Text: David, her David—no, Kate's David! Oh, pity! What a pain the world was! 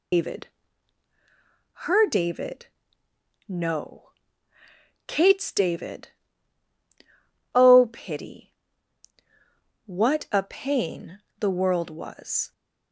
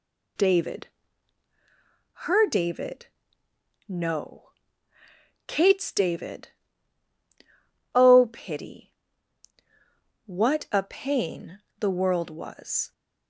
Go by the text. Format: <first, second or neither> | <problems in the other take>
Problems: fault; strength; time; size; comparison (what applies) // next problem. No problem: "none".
second | loses the start of "David"; at 0.1 s; 145 ms // pauses between "pain" and "the"; slight; at 11.1 s; 0.20 s long; slight in the second